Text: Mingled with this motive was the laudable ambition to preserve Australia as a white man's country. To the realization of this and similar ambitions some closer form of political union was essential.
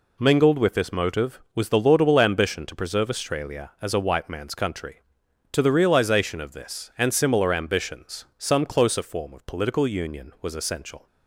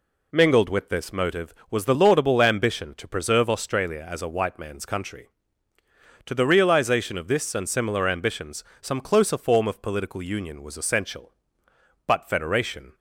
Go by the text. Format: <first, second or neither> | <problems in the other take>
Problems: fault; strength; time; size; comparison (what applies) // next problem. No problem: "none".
first | pauses between "ambitions" and "some"; slight; at 8.6 s; 0.16 s long // goes on to say "But Federation"; noticeable; from 12.0 s on; 0.88 s long